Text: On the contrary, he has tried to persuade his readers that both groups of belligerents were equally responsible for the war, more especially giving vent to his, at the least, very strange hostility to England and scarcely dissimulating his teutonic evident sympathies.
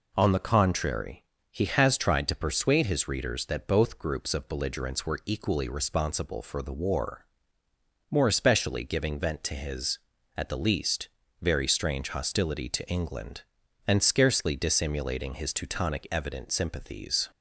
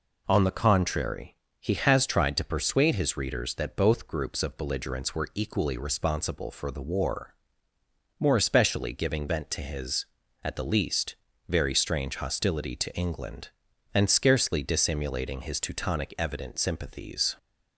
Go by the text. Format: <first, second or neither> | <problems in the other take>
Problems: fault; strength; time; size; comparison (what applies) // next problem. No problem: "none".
neither | none